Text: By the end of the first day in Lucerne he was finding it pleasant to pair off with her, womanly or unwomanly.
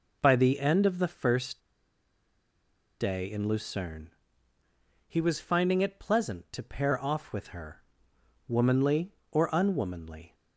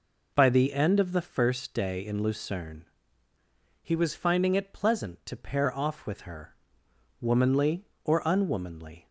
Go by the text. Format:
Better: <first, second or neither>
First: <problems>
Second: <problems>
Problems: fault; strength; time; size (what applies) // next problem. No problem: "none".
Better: second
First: pauses between "first" and "day"; strong; at 1.5 s; 1.4 s long // pauses between "Lucerne" and "he"; noticeable; at 4.0 s; 0.98 s long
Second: pauses between "Lucerne" and "he"; noticeable; at 2.8 s; 0.98 s long